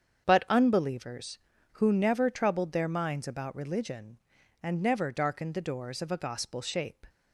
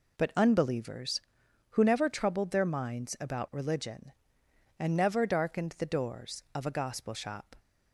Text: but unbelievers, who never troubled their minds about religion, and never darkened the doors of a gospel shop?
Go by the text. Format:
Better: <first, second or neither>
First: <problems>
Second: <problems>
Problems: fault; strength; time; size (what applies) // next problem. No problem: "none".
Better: second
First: starts louder than the rest; strong; until 1.3 s; 7.5 dB // says "shape" for "shop"; at 6.6 s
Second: none